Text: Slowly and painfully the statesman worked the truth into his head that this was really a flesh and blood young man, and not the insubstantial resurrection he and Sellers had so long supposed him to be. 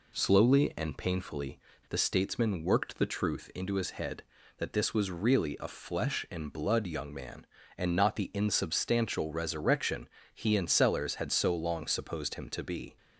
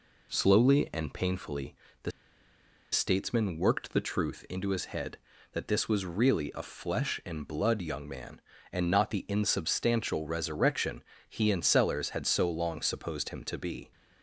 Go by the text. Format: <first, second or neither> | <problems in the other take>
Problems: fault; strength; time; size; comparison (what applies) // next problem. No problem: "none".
first | pauses between "painfully" and "the"; slight; at 1.7 s; 0.30 s long; slight in the first // pauses between "the" and "statesman"; noticeable; at 2.1 s; 0.82 s long // pauses between "resurrection" and "he"; slight; at 11.0 s; 0.24 s long; slight in the first